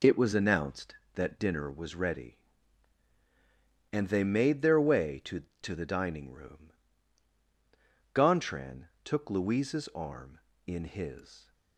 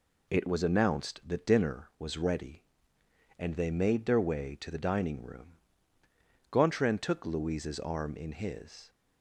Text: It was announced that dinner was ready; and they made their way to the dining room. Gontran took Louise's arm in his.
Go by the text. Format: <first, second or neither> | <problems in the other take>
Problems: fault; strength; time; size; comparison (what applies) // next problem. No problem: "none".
second | says "to" twice; at 5.6 s // pauses between "Gontran" and "took"; slight; at 8.8 s; 0.16 s long